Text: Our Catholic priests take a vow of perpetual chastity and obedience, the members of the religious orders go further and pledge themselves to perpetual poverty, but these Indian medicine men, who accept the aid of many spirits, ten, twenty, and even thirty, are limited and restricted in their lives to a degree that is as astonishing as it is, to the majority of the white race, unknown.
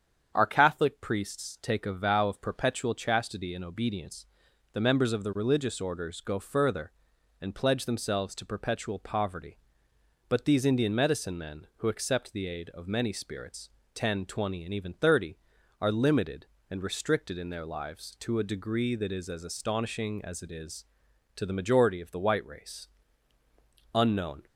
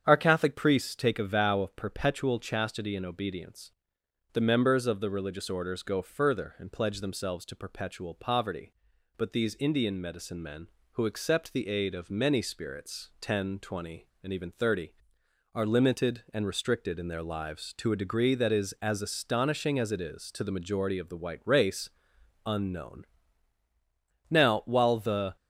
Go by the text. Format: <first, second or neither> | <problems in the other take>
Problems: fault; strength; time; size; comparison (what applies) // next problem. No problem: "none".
first | starts louder than the rest; strong; until 1.0 s; 8 dB; strong in the first // goes on to say "Now while the"; noticeable; from 24.2 s on; 1.0 s long